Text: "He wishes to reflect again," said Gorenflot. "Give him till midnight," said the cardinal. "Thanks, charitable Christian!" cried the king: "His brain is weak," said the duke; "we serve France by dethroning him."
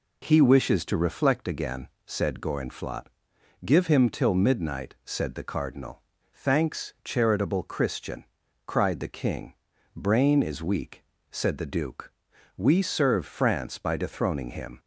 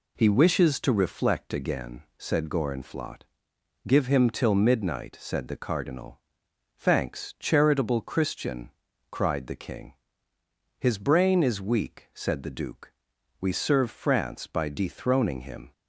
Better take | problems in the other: second | skips "His"; at 9.7 s

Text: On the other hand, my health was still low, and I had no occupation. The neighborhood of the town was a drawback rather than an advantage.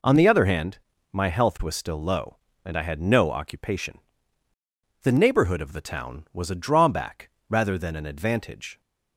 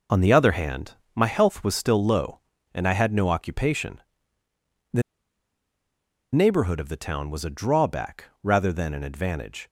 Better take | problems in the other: first | pauses between "The" and "neighborhood"; strong; at 5.0 s; 1.3 s long // pauses between "drawback" and "rather"; slight; at 8.2 s; 0.18 s long; slight in the first

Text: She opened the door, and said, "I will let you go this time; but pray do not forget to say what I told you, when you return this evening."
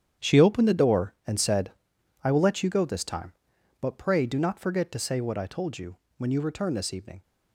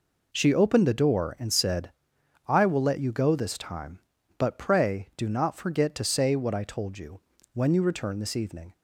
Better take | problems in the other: second | gets quieter; strong; throughout; 12 dB

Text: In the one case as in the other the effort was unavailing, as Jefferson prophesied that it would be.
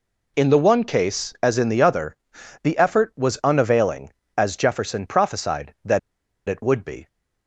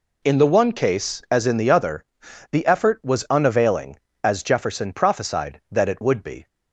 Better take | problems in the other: second | pauses between "other" and "the"; noticeable; at 2.1 s; 0.48 s long; noticeable in the second // pauses between "that" and "it"; noticeable; at 5.9 s; 0.49 s long

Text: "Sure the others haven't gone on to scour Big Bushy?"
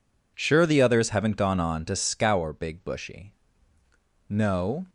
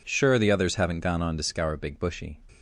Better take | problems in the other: second | goes on to say "No"; from 4.2 s on; 0.60 s long

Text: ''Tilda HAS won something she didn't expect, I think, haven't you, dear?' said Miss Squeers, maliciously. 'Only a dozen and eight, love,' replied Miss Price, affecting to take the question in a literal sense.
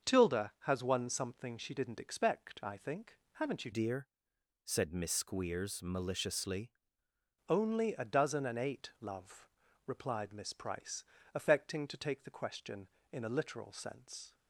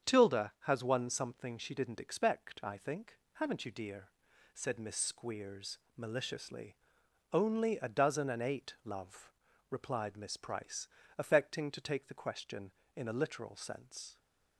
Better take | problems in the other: second | starts louder than the rest; until 1.1 s; 6.5 dB; strong in the second // changes voice from "dear" to "maliciously"; from 3.7 to 6.7 s; 3.0 s long

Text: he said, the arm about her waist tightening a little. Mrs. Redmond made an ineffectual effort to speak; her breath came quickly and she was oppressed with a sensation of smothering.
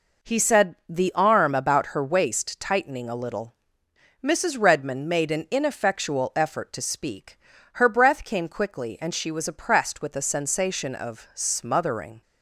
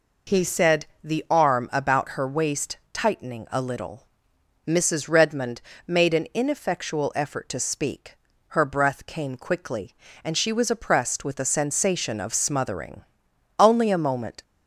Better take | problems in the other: first | pauses between "waist" and "tightening"; slight; at 2.7 s; 0.16 s long // pauses between "Redmond" and "made"; slight; at 5.6 s; 0.24 s long // goes on to say "Only a moment"; noticeable; from 13.5 s on; 0.84 s long

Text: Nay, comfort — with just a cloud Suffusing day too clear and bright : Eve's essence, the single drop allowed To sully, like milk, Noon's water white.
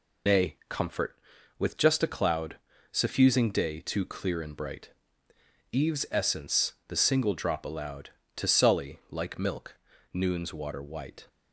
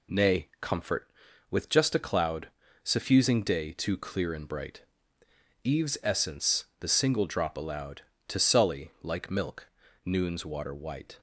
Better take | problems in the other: second | loses the start of "Nay"; at 0.2 s; 90 ms // pauses between "cloud" and "Suffusing"; slight; at 2.5 s; 0.34 s long; slight in the second

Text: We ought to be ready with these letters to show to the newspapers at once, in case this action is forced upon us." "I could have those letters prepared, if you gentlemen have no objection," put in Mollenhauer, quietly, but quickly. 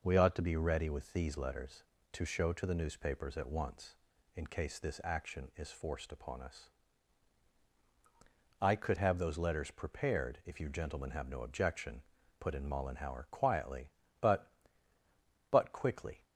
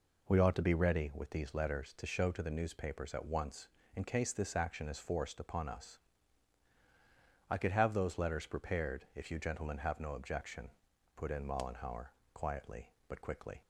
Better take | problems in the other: second | says "but" twice; at 15.5 s

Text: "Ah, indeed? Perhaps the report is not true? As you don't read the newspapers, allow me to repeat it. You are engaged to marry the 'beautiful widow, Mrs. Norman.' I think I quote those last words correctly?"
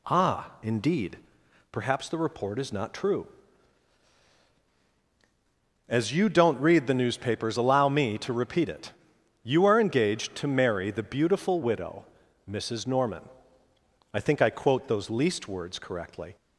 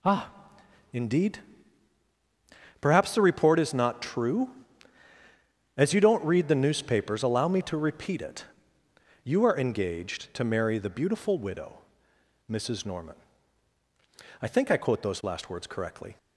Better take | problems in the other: second | says "least" for "last"; at 15.0 s

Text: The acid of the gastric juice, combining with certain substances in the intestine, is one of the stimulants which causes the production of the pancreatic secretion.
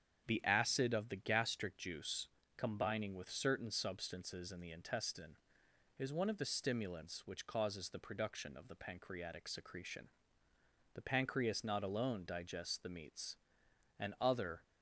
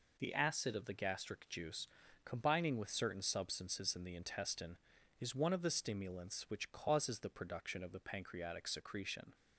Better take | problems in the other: second | starts louder than the rest; strong; until 1.2 s; 8 dB // goes on to say "The pancreas not alone digests the meats and other"; strong; from 10.9 s on; 3.7 s long

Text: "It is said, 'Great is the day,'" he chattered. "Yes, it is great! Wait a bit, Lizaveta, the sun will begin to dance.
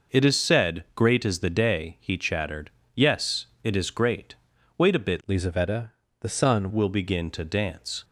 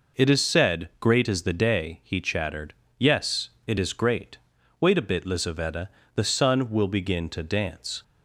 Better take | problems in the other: second | changes voice from "Lizaveta" to "sun"; from 5.2 to 6.6 s; 1.4 s long

